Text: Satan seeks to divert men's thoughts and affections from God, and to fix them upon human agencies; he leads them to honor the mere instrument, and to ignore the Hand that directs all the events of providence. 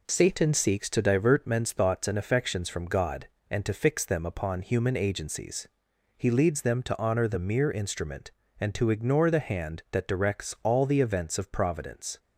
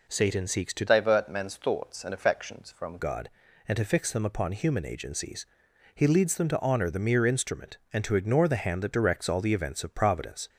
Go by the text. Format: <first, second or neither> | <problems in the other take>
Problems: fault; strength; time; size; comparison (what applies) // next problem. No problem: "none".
first | changes voice from "divert" to "from"; from 0.8 to 2.9 s; 2.1 s long